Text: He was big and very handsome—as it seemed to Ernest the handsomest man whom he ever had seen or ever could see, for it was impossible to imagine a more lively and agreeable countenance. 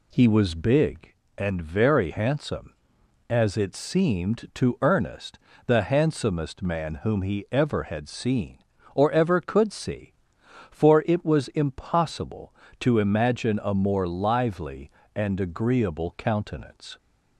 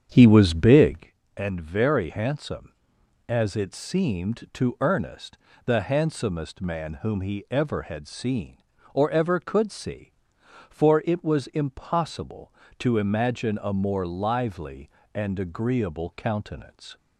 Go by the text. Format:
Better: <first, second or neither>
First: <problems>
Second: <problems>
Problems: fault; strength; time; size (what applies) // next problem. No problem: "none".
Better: first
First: pauses between "Ernest" and "the"; slight; at 5.3 s; 0.30 s long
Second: starts louder than the rest; strong; until 1.1 s; 8 dB // pauses between "Ernest" and "the"; slight; at 5.3 s; 0.30 s long